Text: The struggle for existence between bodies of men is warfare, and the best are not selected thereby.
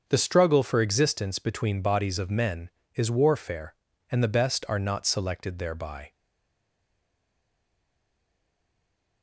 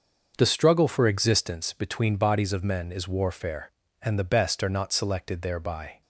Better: second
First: starts louder than the rest; until 1.0 s; 7 dB // stays silent after the last word; strong; from 6.1 s on; 3.1 s long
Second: starts louder than the rest; until 1.3 s; 6.5 dB

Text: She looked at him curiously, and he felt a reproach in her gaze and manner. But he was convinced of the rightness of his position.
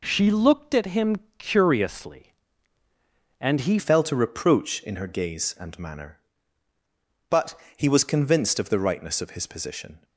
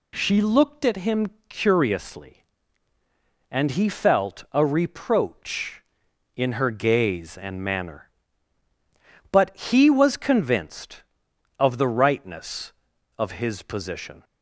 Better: second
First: pauses between "him" and "curiously"; slight; at 1.1 s; 0.22 s long // changes voice at "felt"; from 3.7 s on; 6.3 s long // pauses between "But" and "he"; slight; at 7.5 s; 0.20 s long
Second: pauses between "him" and "curiously"; slight; at 1.2 s; 0.22 s long

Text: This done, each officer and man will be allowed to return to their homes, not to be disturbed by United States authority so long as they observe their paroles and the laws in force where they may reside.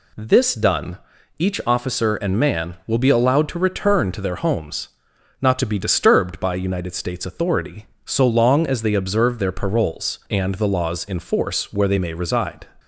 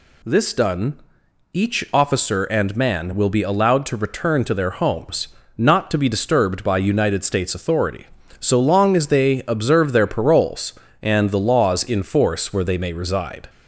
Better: neither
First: none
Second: none

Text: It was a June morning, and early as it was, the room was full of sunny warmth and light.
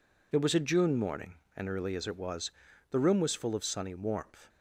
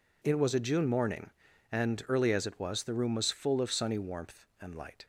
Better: second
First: stops before "and light"; at 4.4 s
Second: none

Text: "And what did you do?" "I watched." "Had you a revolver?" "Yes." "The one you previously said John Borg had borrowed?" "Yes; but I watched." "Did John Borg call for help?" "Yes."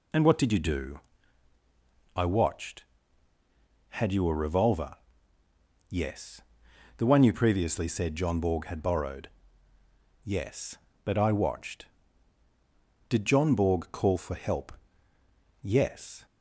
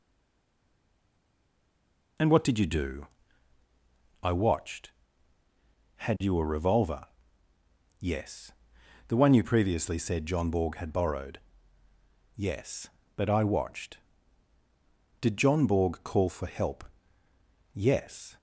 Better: first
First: none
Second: stays silent before the first word; until 2.1 s; 2.1 s long

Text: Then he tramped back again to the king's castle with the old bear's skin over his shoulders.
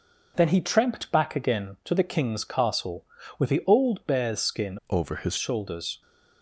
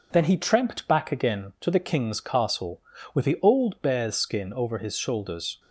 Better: second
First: changes voice from "over" to "his"; from 4.8 to 5.3 s; 0.5 s long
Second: none

